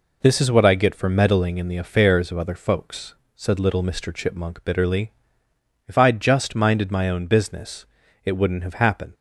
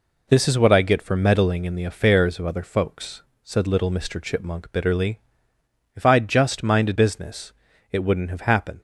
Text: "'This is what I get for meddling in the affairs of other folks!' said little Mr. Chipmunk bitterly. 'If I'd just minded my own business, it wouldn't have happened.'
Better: first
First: none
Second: skips "my own"; at 6.9 s

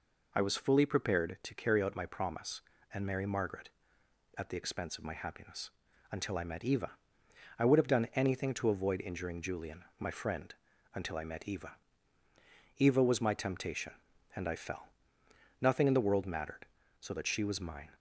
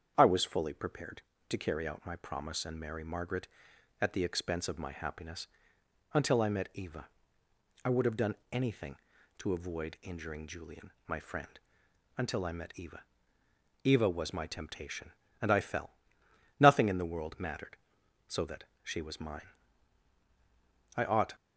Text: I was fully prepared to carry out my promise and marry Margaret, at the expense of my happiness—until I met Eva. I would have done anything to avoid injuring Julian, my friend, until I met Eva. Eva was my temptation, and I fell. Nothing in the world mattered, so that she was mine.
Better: first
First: none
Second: starts louder than the rest; strong; until 1.1 s; 7.5 dB // pauses between "done" and "anything"; slight; at 8.3 s; 0.16 s long // pauses between "that" and "she"; slight; at 18.6 s; 0.18 s long // goes on to say "I ought"; slight; from 20.9 s on; 0.40 s long

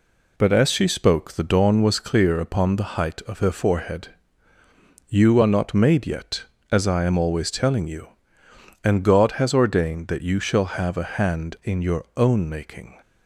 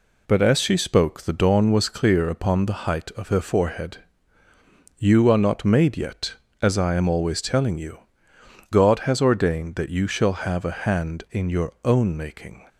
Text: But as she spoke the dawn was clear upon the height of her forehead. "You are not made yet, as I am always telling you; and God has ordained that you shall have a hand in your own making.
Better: first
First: none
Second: skips "and"; at 8.3 s

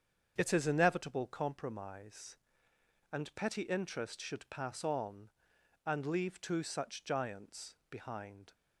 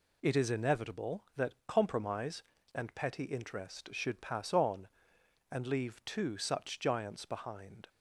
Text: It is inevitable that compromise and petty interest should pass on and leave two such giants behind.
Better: second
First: starts louder than the rest; strong; until 1.3 s; 7.5 dB // skips "that"; at 1.2 s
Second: none

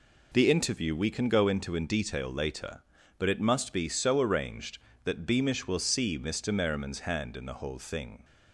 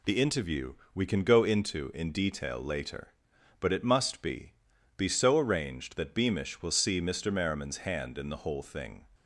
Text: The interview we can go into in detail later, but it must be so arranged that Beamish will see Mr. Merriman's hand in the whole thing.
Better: first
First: none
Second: pauses between "interview" and "we"; slight; at 0.7 s; 0.22 s long // says "be" twice; at 4.9 s

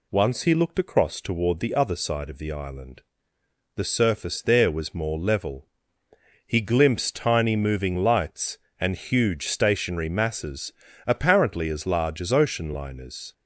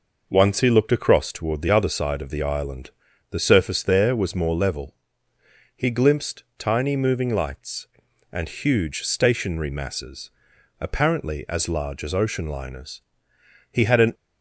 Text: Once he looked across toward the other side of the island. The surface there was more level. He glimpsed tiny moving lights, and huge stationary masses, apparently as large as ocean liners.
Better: first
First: none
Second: goes on to say "He had an"; slight; from 13.7 s on; 0.42 s long

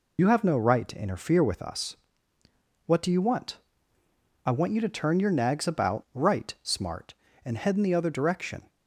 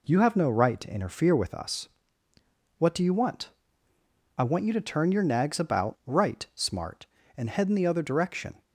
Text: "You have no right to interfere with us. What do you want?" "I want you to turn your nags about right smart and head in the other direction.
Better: second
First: loses the start of "You"; at 0.1 s; 60 ms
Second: none

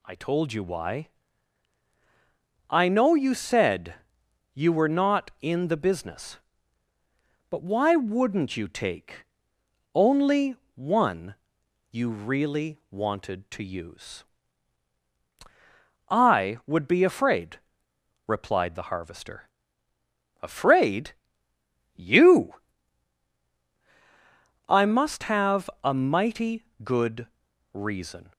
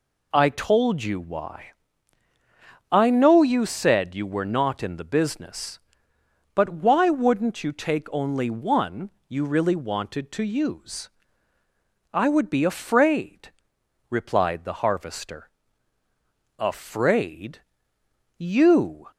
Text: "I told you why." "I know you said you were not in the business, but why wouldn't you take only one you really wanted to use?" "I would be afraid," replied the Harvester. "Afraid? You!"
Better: second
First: pauses between "said" and "you"; noticeable; at 3.9 s; 0.58 s long // pauses between "take" and "only"; noticeable; at 9.2 s; 0.70 s long // pauses between "only" and "one"; slight; at 10.5 s; 0.18 s long // pauses between "one" and "you"; noticeable; at 11.3 s; 0.56 s long // goes on to say "I must have a mighty good reason"; strong; from 24.6 s on; 3.6 s long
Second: pauses between "one" and "you"; slight; at 9.1 s; 0.16 s long

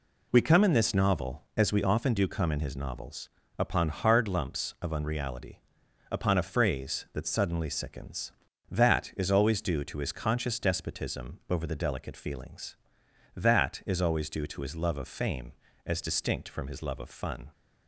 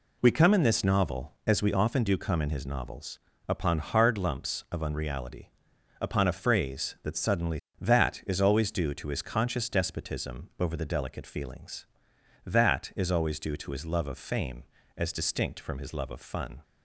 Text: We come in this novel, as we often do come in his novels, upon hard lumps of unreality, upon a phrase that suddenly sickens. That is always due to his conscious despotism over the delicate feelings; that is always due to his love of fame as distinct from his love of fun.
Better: first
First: none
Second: skips "sickens"; at 7.6 s

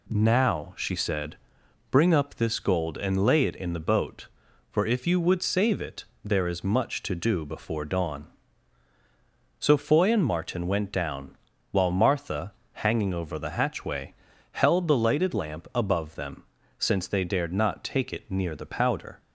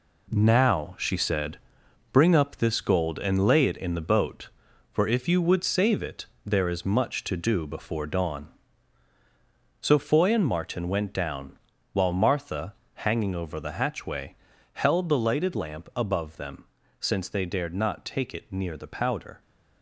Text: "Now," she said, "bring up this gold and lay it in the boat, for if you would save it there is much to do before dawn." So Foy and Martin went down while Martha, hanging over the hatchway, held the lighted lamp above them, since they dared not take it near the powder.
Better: first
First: pauses between "it" and "there"; slight; at 6.0 s; 0.18 s long // pauses between "down" and "while"; slight; at 11.3 s; 0.36 s long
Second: gets quieter; strong; throughout; 8 dB // pauses between "it" and "there"; slight; at 6.2 s; 0.18 s long // pauses between "down" and "while"; slight; at 11.5 s; 0.36 s long

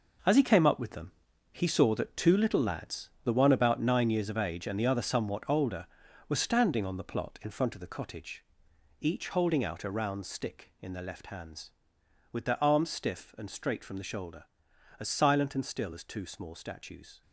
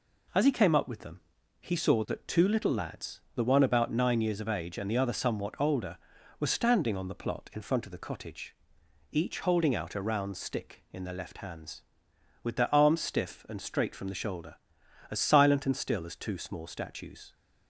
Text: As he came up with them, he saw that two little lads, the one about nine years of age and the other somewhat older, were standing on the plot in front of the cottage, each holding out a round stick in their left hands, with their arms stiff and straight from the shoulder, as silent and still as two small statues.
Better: second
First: gets quieter; strong; throughout; 9.5 dB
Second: none

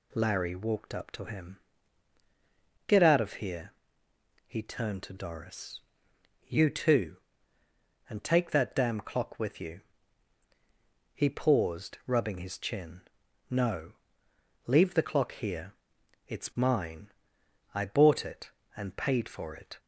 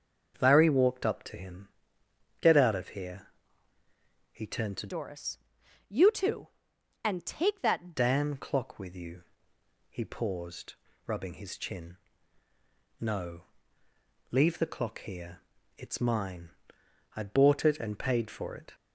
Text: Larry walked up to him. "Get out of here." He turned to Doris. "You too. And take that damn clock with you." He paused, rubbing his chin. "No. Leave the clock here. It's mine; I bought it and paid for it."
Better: first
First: none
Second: starts louder than the rest; until 1.4 s; 6.5 dB // changes voice from "Doris" to "that"; from 4.8 to 7.9 s; 3.1 s long

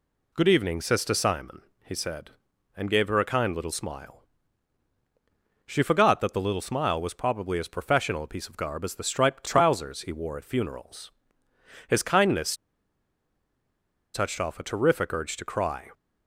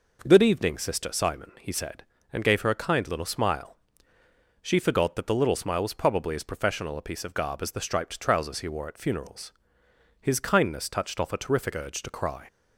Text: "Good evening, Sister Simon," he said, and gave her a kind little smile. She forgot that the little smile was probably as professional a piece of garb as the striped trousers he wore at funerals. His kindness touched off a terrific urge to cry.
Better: second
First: pauses between "kindness" and "touched"; strong; at 12.5 s; 1.5 s long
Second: none

